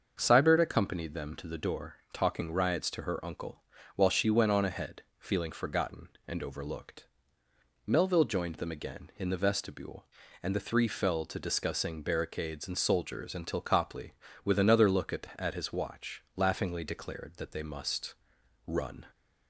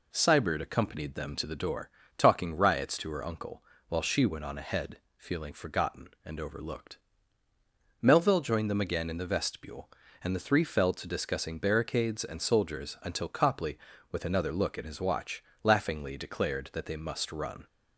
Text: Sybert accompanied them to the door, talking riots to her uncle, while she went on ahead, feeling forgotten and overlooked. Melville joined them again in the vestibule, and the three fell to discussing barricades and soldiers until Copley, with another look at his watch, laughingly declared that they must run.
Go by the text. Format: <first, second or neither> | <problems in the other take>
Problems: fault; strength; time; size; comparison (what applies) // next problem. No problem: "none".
second | starts louder than the rest; until 1.2 s; 6.5 dB // says "at" twice; at 15.3 s // pauses between "must" and "run"; noticeable; at 18.1 s; 0.50 s long